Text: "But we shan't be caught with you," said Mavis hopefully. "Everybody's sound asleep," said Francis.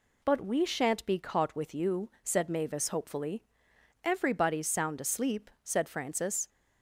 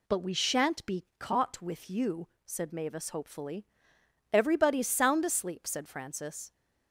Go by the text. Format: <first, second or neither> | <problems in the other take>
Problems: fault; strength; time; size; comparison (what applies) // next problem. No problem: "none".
neither | none